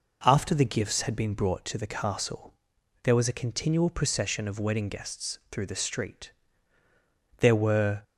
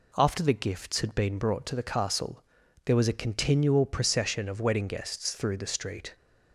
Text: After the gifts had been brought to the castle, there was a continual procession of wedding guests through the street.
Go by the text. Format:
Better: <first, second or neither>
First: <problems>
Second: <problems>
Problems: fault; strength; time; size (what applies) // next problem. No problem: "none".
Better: second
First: goes on to say "There were"; noticeable; from 7.3 s on; 0.64 s long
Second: none